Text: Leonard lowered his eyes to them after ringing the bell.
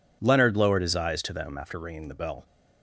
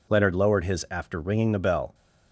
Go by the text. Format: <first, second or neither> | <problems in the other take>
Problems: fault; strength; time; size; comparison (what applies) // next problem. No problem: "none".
first | skips "eyes to them"; at 0.8 s